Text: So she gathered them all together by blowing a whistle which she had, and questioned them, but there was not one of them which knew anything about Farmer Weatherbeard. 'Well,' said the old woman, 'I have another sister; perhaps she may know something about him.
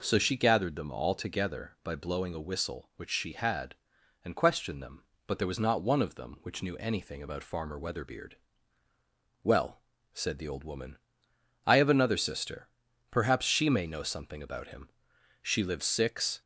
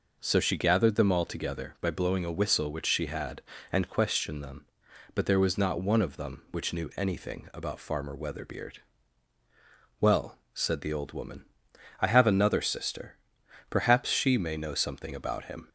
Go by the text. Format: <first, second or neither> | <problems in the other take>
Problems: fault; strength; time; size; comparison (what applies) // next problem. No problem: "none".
second | goes on to say "She lives six"; noticeable; from 15.4 s on; 0.98 s long